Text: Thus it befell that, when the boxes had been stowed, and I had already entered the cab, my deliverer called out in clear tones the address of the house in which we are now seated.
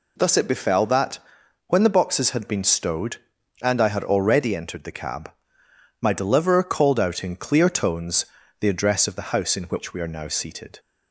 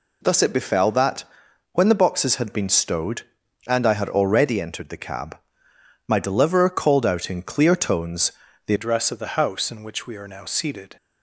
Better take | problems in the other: first | pauses between "tones" and "the"; slight; at 8.3 s; 0.34 s long; slight in the first // changes voice at "address"; from 8.7 s on; 2.2 s long

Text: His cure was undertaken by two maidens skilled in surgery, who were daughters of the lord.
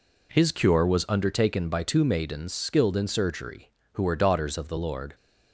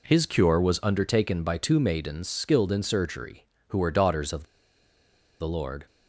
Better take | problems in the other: first | pauses between "of" and "the"; noticeable; at 4.4 s; 0.97 s long

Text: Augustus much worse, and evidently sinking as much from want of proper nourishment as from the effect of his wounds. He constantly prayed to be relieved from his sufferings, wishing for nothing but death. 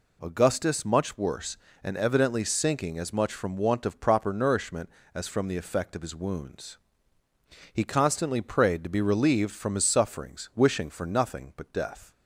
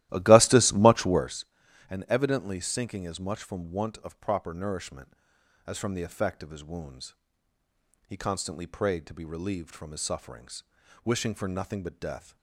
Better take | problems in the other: first | starts louder than the rest; strong; until 1.4 s; 15 dB

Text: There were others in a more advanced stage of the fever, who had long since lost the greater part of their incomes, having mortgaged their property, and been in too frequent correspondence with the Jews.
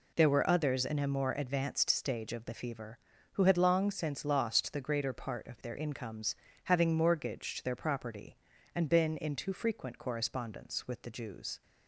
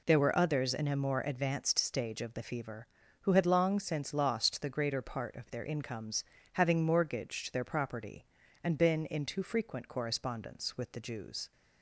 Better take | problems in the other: neither | none

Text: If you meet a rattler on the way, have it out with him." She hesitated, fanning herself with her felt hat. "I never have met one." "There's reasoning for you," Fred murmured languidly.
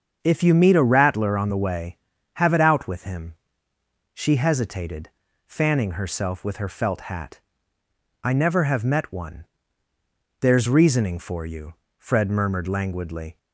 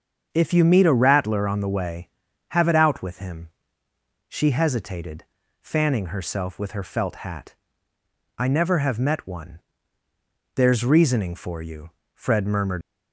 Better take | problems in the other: first | starts louder than the rest; until 1.3 s; 7 dB; also in the first // stops before "languidly"; at 12.8 s

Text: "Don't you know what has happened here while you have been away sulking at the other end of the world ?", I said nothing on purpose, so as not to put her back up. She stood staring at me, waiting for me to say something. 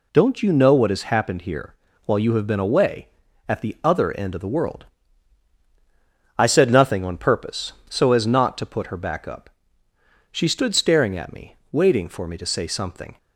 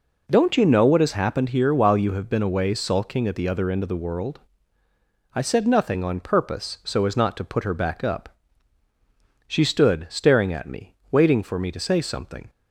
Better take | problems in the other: second | pauses between "here" and "while"; slight; at 1.7 s; 0.30 s long // skips "sulking"; at 3.2 s

